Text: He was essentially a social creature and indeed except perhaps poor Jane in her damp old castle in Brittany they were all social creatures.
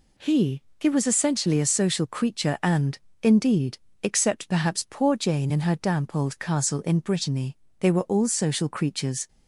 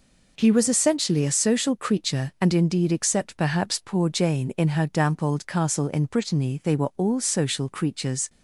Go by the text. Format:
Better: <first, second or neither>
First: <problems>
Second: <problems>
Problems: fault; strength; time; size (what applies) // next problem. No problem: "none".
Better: second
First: says "He" twice; at 0.7 s // pauses between "and" and "indeed"; slight; at 2.9 s; 0.24 s long // pauses between "indeed" and "except"; slight; at 3.7 s; 0.26 s long // pauses between "Brittany" and "they"; slight; at 7.5 s; 0.24 s long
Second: none